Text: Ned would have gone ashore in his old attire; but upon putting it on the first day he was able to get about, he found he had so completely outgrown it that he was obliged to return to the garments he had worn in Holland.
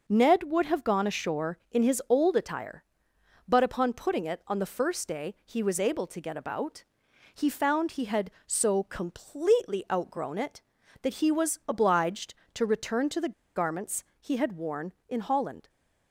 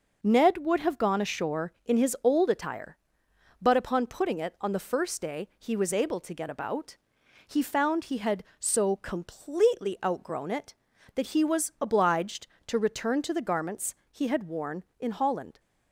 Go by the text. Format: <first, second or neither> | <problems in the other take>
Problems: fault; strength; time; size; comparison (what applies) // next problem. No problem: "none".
second | pauses between "the" and "garments"; slight; at 13.3 s; 0.23 s long // pauses between "garments" and "he"; slight; at 14.0 s; 0.18 s long; slight in the second